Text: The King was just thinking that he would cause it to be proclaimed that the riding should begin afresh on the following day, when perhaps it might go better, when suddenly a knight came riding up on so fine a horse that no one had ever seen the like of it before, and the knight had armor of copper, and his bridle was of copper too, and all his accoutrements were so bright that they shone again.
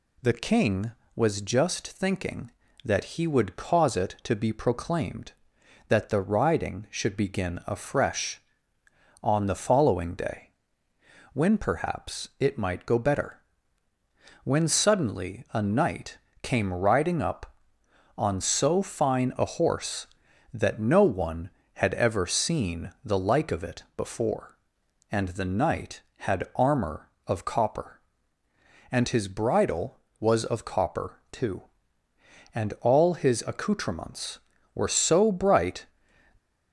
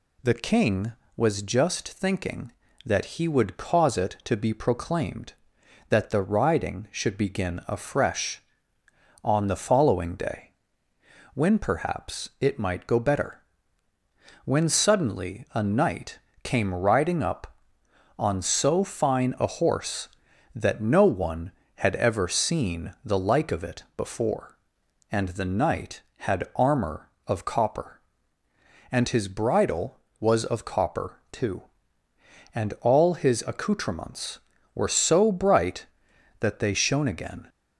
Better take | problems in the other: second | pauses between "knight" and "came"; slight; at 16.1 s; 0.24 s long; slight in the second // stops before "that they shone again"; at 36.3 s

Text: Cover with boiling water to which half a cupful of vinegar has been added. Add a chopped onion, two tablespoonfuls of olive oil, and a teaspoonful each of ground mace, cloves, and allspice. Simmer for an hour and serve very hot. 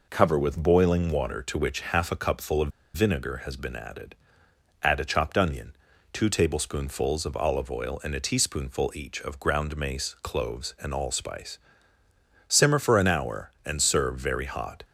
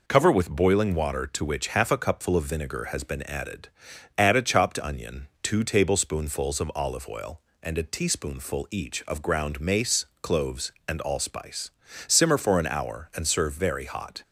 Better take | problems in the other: second | pauses between "of" and "vinegar"; slight; at 2.7 s; 0.24 s long

